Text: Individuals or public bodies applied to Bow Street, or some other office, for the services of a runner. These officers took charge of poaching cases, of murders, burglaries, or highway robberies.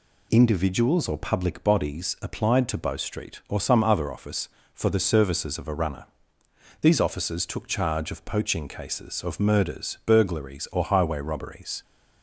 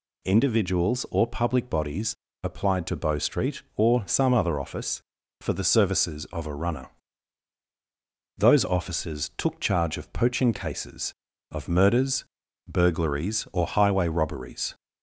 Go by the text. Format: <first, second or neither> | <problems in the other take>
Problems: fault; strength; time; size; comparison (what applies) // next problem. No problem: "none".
first | pauses between "bodies" and "applied"; slight; at 2.1 s; 0.30 s long // says "Those" for "These"; at 8.3 s